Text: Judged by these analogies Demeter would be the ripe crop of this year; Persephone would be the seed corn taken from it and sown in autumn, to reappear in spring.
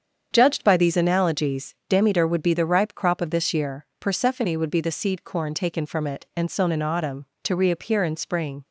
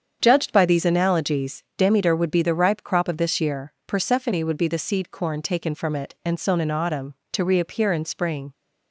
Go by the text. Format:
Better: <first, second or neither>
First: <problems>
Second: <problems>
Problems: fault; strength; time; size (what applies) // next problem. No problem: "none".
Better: neither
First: starts louder than the rest; strong; until 1.3 s; 7.5 dB // pauses between "analogies" and "Demeter"; slight; at 1.7 s; 0.16 s long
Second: starts louder than the rest; strong; until 1.2 s; 7.5 dB // pauses between "analogies" and "Demeter"; slight; at 1.6 s; 0.16 s long